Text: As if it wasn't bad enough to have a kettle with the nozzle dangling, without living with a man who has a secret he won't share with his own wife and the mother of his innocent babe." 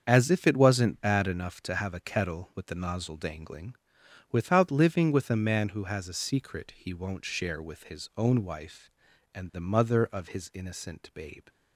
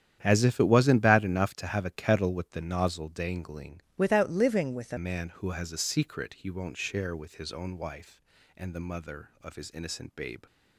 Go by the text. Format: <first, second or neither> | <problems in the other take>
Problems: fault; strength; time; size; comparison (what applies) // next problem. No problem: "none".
first | starts louder than the rest; strong; until 1.2 s; 9.5 dB; also in the first // changes voice from "without" to "a"; from 3.9 to 4.9 s; 1.0 s long